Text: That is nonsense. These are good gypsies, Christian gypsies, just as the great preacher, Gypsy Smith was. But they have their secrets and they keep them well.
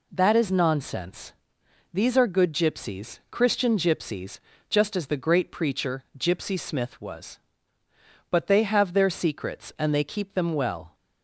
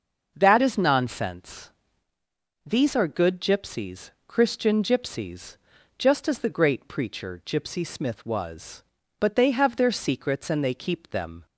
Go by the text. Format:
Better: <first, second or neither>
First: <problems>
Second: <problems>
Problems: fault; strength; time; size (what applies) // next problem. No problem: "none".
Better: first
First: none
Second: starts louder than the rest; until 1.3 s; 6.5 dB // stops before "well"; at 11.4 s